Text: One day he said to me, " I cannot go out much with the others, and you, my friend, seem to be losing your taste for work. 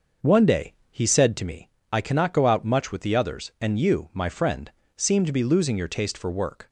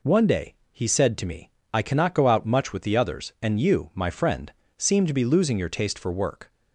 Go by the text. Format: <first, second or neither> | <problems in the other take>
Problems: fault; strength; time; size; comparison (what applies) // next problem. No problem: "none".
second | starts louder than the rest; until 1.4 s; 6 dB // pauses between "day" and "he"; slight; at 0.7 s; 0.16 s long; slight in the second